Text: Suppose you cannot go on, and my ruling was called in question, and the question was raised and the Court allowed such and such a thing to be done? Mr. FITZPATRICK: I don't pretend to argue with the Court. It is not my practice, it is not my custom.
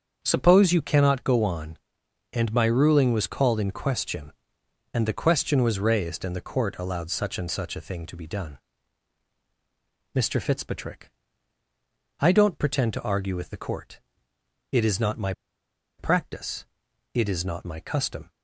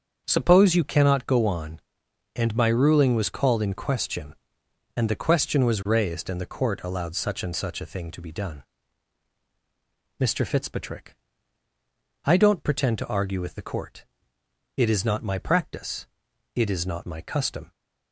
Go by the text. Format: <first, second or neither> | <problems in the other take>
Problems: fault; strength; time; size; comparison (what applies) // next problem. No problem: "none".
second | starts louder than the rest; until 1.2 s; 7 dB; strong in the second // pauses between "my" and "practice"; noticeable; at 15.3 s; 0.66 s long